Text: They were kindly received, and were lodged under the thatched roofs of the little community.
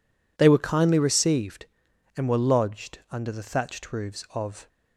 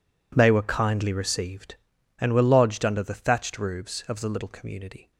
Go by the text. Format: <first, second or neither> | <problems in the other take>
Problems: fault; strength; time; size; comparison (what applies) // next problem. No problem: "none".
second | stops before "the little community"; at 4.6 s